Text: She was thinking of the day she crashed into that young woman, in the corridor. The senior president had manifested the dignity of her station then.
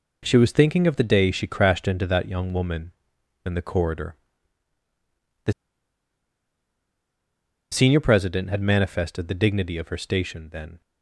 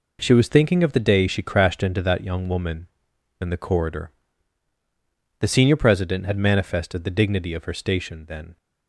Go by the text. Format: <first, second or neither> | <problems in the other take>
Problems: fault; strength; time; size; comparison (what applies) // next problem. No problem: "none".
second | pauses between "The" and "senior"; strong; at 5.5 s; 2.1 s long